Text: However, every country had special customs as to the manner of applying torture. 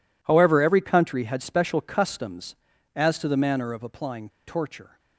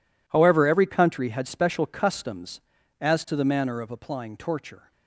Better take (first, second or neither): second